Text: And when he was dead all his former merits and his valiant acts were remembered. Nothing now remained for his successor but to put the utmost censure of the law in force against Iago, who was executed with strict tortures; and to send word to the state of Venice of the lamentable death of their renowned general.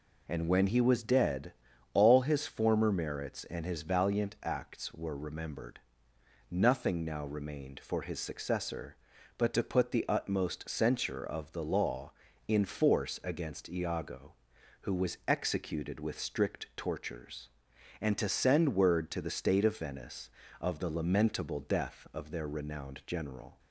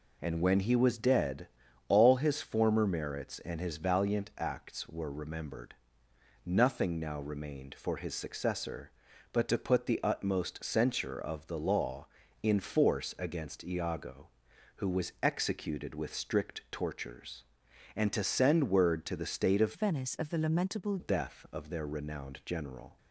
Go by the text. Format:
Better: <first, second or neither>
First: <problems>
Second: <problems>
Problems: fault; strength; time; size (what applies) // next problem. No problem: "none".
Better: first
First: pauses between "dead" and "all"; at 1.5 s; 0.42 s long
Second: pauses between "dead" and "all"; at 1.4 s; 0.42 s long // changes voice from "Venice" to "lamentable"; from 19.7 to 20.9 s; 1.2 s long